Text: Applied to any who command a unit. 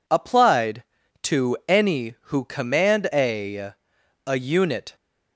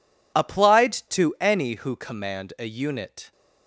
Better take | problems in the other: second | says "a" twice; at 4.2 s

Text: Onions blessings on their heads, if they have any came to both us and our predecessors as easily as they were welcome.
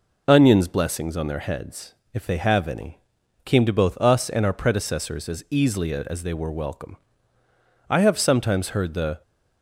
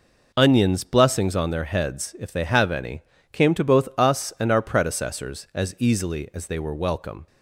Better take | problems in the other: second | pauses between "any" and "came"; at 2.9 s; 0.44 s long; slight in the second // goes on to say "I have sometimes heard the"; from 7.8 s on; 1.3 s long

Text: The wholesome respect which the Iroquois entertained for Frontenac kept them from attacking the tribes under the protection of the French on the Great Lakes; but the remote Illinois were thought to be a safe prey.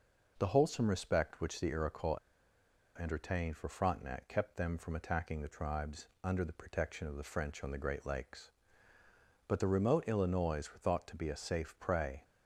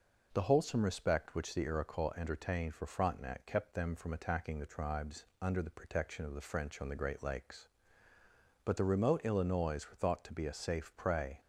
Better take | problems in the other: second | pauses between "Iroquois" and "entertained"; noticeable; at 2.1 s; 0.80 s long // pauses between "tribes" and "under"; slight; at 6.0 s; 0.16 s long; slight in the second

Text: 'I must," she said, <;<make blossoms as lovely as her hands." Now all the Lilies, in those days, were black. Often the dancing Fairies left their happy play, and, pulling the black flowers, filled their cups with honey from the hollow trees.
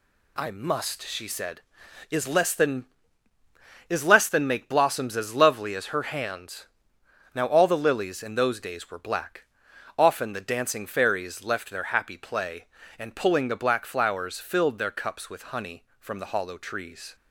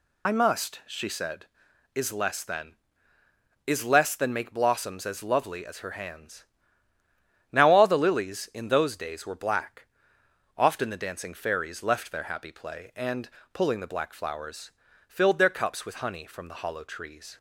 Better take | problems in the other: first | loses the start of "I"; at 0.2 s; 55 ms

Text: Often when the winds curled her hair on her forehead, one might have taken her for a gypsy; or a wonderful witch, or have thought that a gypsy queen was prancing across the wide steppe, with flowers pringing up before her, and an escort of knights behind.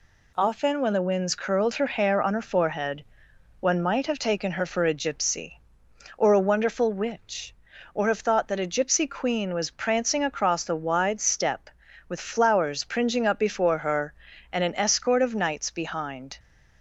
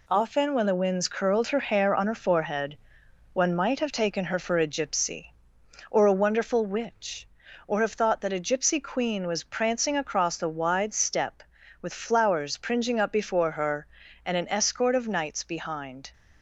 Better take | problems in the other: first | gets quieter; noticeable; throughout; 4.5 dB

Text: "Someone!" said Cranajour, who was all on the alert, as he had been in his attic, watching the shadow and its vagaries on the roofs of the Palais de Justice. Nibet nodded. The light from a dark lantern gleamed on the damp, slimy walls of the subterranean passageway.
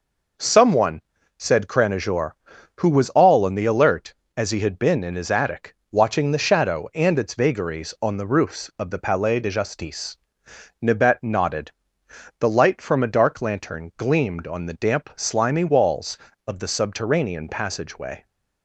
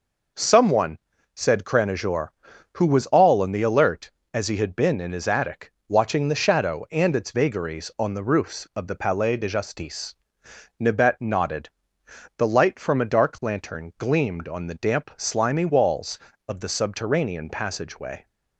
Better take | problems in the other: neither | none

